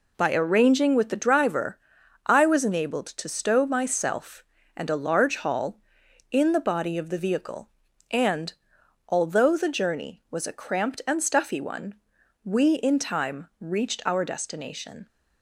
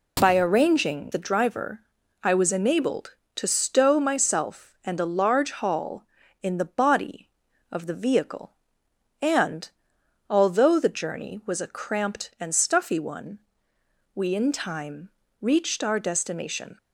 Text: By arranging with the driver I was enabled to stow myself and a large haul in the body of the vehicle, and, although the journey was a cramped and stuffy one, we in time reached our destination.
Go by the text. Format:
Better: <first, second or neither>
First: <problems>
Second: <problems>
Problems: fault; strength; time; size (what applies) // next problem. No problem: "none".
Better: first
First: pauses between "driver" and "I"; noticeable; at 1.7 s; 0.48 s long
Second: skips "with"; at 1.1 s // pauses between "driver" and "I"; at 1.8 s; 0.42 s long // pauses between "time" and "reached"; slight; at 15.0 s; 0.32 s long